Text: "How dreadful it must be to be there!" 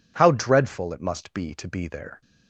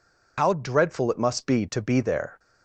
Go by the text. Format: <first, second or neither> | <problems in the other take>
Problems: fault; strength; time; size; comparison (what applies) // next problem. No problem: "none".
first | loses the start of "How"; at 0.3 s; 130 ms